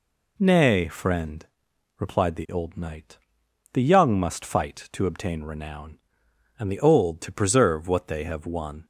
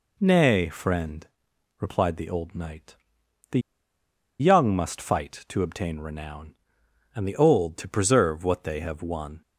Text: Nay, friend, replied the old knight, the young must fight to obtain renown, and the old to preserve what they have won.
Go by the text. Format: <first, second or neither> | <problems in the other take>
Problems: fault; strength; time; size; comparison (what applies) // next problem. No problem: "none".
first | pauses between "the" and "young"; noticeable; at 3.6 s; 0.78 s long